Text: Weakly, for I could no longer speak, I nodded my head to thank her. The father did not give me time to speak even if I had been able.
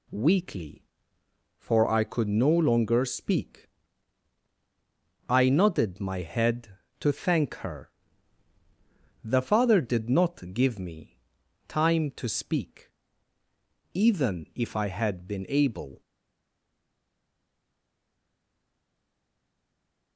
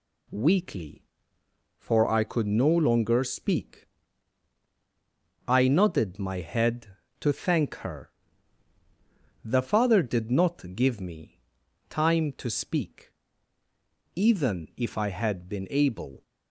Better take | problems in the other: second | pauses between "me" and "time"; noticeable; at 11.1 s; 0.50 s long; noticeable in the second // pauses between "speak" and "even"; at 12.9 s; 1.0 s long; also in the second // stays silent after the last word; strong; from 16.0 s on; 4.1 s long

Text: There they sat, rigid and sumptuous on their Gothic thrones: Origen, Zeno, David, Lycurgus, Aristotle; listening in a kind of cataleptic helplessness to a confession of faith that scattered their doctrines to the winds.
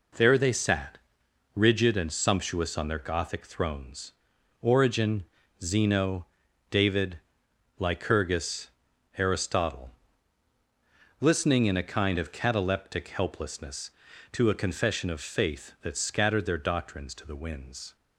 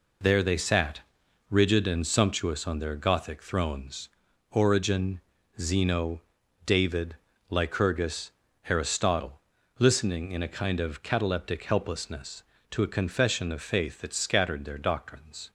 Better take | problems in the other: first | stops before "to the winds"; at 15.4 s

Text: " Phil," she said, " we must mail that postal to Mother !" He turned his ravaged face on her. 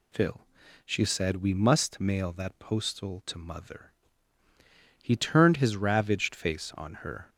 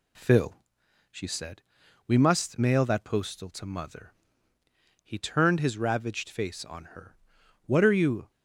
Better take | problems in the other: first | goes on to say "What are you"; noticeable; from 7.6 s on; 0.64 s long

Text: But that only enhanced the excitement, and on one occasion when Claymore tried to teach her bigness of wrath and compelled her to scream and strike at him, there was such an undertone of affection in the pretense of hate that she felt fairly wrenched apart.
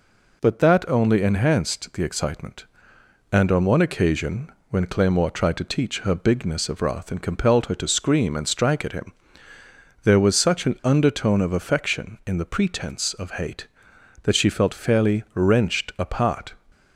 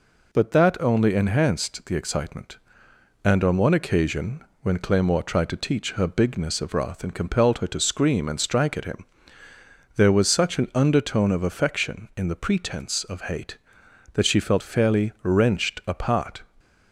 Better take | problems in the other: neither | pauses between "occasion" and "when"; slight; the same in both

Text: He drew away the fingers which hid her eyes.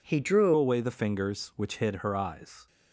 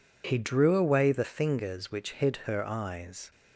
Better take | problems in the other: second | changes voice at "away"; from 0.5 s on; 2.1 s long

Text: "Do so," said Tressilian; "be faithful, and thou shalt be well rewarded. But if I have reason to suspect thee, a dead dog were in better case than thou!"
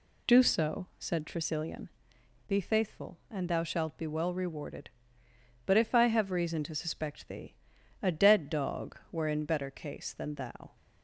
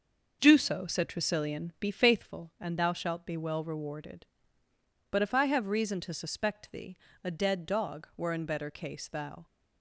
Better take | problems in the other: first | starts louder than the rest; noticeable; until 1.4 s; 6 dB // skips "than"; at 9.0 s

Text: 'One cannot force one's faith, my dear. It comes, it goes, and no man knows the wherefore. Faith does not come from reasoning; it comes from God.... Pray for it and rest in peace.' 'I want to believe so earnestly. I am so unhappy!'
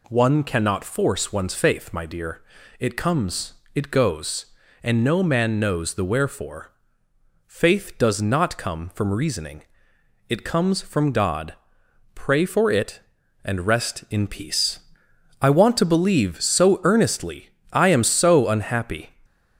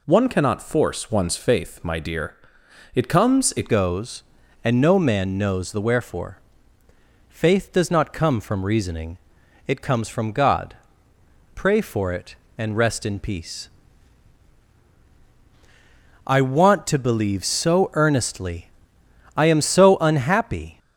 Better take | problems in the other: first | changes voice at "goes"; from 3.6 s on; 17.1 s long

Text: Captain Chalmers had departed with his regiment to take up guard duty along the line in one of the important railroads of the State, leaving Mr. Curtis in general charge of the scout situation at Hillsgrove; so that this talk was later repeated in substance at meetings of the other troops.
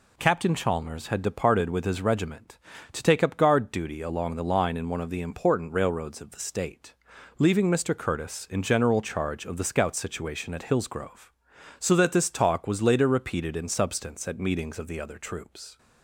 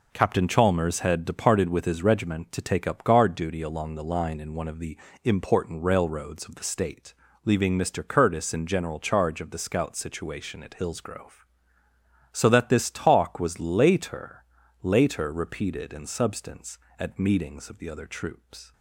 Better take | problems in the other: first | pauses between "the" and "important"; slight; at 4.9 s; 0.26 s long // says "later" twice; at 14.8 s

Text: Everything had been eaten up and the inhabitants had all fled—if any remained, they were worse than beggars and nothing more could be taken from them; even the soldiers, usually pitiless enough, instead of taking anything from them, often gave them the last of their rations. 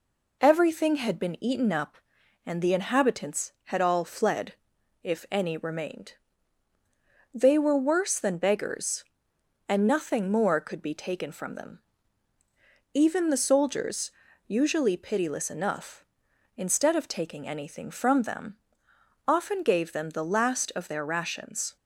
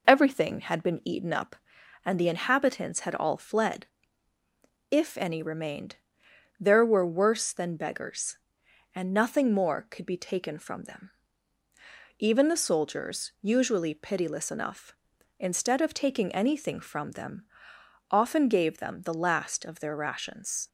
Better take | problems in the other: first | says "there" for "they"; at 6.5 s

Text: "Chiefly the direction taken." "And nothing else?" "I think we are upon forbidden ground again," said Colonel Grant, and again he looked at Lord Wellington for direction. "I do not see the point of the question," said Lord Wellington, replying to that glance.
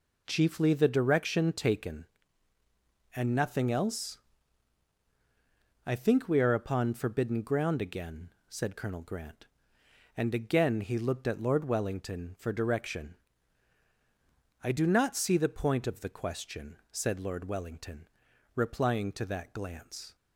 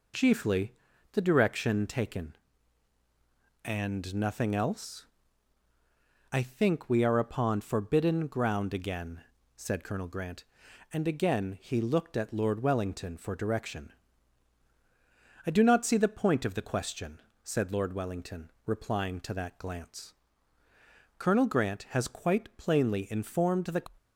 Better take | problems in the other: first | pauses between "Chiefly" and "the"; slight; at 0.7 s; 0.34 s long // goes on to say "Colonel Grant has quite plainly informed the"; strong; from 21.1 s on; 2.6 s long

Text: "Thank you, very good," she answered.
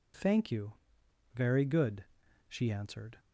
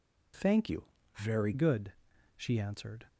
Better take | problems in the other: first | changes voice from "you" to "very"; from 0.6 to 1.5 s; 0.9 s long

